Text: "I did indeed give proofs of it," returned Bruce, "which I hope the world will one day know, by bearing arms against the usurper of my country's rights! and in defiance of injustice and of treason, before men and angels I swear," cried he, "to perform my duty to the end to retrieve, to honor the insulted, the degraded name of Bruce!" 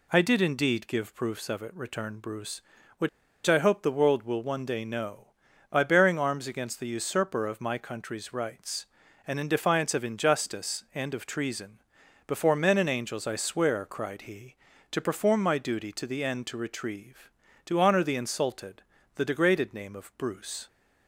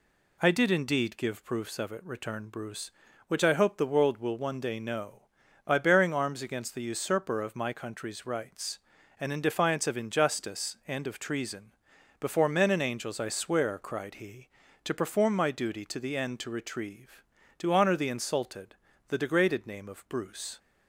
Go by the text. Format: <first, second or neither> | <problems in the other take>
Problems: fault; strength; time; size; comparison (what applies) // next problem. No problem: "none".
second | pauses between "which" and "I"; at 3.0 s; 0.37 s long